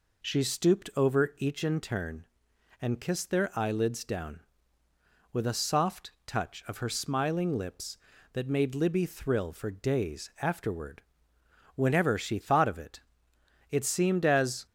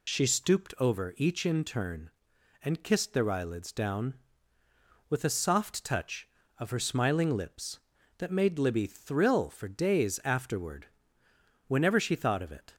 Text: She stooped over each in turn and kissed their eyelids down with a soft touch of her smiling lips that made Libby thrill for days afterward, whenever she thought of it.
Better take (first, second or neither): second